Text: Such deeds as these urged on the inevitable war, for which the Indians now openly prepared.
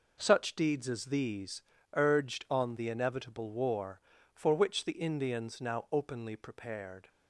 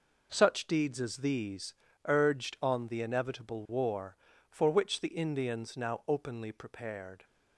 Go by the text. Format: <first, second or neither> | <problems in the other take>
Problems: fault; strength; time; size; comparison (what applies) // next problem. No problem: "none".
neither | pauses between "these" and "urged"; slight; the same in both